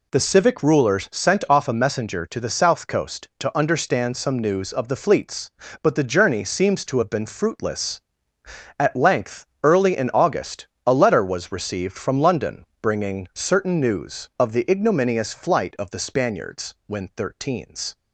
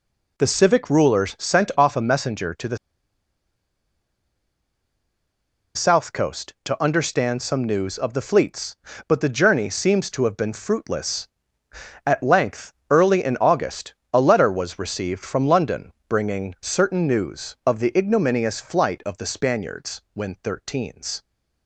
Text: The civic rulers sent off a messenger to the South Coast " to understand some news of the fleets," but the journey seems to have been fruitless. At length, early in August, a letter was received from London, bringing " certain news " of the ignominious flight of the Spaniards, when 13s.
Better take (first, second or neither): first